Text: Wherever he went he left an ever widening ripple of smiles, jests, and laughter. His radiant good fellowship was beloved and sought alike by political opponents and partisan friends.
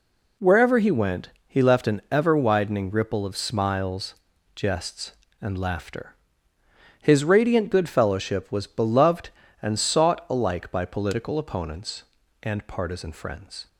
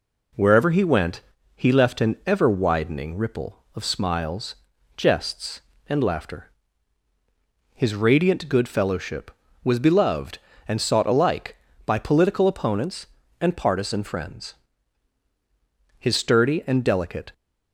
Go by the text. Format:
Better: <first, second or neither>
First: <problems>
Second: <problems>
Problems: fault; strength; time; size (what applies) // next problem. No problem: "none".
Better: first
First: pauses between "went" and "he"; slight; at 1.2 s; 0.18 s long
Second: pauses between "went" and "he"; slight; at 1.2 s; 0.34 s long // goes on to say "His sturdy and delicate"; from 15.9 s on; 1.3 s long